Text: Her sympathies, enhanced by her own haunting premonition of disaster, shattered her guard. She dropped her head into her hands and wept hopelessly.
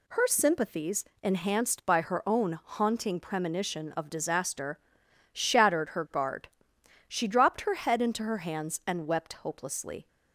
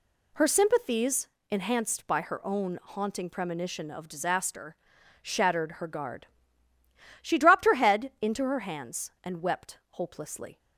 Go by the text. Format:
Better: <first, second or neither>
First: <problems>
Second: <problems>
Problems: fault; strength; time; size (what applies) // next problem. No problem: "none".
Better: neither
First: none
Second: none